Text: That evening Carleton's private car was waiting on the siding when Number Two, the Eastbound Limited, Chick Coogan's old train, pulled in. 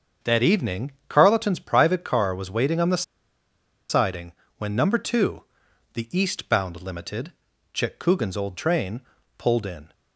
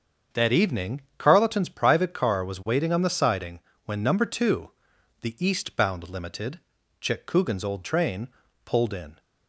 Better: second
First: starts louder than the rest; until 1.4 s; 7 dB // pauses between "evening" and "Carleton's"; slight; at 0.9 s; 0.16 s long // pauses between "the" and "siding"; noticeable; at 3.0 s; 0.86 s long // pauses between "siding" and "when"; slight; at 4.3 s; 0.26 s long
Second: starts louder than the rest; until 1.4 s; 7 dB // pauses between "evening" and "Carleton's"; slight; at 1.0 s; 0.16 s long // pauses between "siding" and "when"; slight; at 3.5 s; 0.26 s long

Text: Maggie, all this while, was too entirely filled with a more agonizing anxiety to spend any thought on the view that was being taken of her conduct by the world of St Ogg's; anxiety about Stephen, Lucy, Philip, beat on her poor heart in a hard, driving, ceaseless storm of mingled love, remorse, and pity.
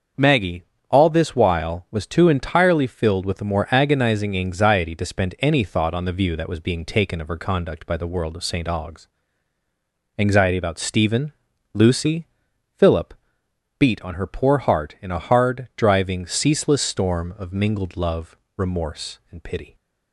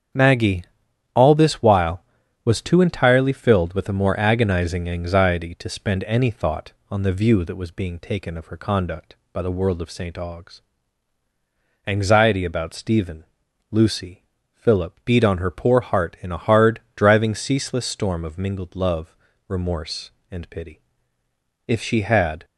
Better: first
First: starts louder than the rest; until 1.4 s; 6.5 dB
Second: starts louder than the rest; strong; until 1.6 s; 8 dB // goes on to say "If she had"; noticeable; from 21.6 s on; 0.78 s long

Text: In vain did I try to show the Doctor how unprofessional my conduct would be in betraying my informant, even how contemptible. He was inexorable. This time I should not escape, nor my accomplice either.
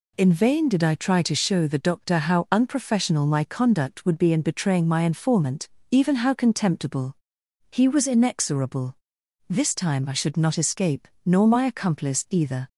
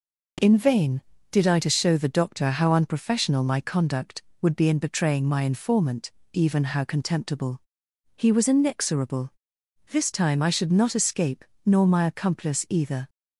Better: first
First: none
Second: skips "try"; at 1.5 s

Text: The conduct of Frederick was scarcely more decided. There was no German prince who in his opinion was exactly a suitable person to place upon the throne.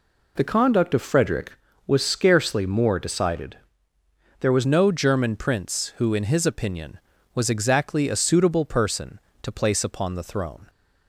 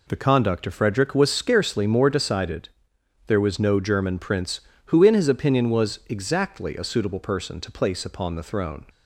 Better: second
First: changes voice at "no"; from 4.6 s on; 6.0 s long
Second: none

